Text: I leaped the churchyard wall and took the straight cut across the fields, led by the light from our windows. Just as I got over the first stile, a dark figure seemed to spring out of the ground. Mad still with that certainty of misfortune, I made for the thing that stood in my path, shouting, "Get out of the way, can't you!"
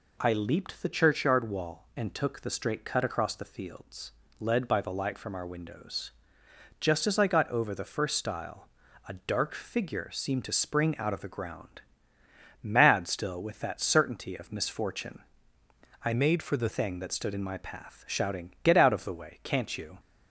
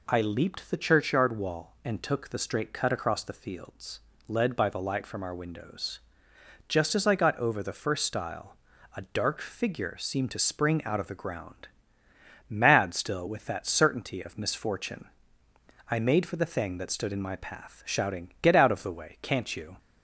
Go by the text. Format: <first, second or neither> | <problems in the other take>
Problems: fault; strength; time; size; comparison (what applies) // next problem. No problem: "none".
second | changes voice from "made" to "the"; from 16.1 to 16.6 s; 0.5 s long